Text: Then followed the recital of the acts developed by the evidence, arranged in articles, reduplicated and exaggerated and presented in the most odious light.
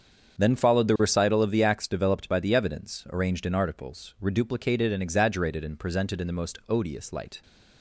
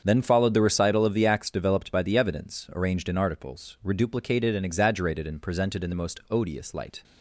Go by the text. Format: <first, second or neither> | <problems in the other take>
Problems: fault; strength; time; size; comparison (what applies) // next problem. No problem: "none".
neither | starts louder than the rest; strong; the same in both